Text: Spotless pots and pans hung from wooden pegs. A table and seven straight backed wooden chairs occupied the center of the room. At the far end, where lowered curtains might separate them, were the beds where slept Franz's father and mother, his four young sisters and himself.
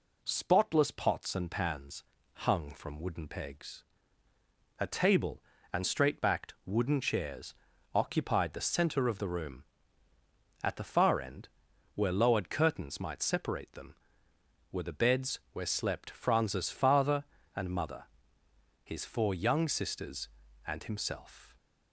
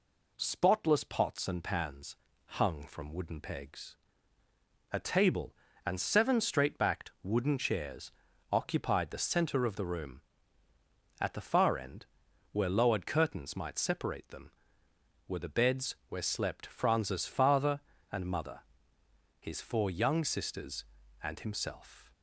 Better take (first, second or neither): second